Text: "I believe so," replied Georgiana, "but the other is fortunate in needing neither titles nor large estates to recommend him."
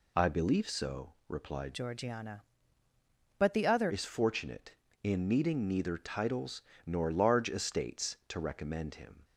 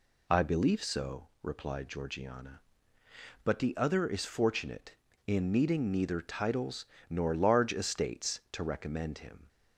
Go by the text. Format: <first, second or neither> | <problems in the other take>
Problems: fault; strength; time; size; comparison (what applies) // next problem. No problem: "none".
second | changes voice from "Georgiana" to "other"; from 1.7 to 3.9 s; 2.2 s long // pauses between "titles" and "nor"; slight; at 6.6 s; 0.24 s long; slight in the second